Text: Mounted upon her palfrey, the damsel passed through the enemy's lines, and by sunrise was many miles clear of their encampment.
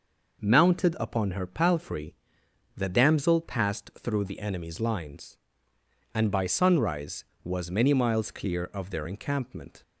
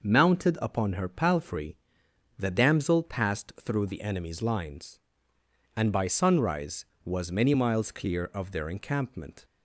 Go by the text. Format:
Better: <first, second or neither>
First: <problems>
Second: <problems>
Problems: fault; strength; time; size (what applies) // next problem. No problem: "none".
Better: neither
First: none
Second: none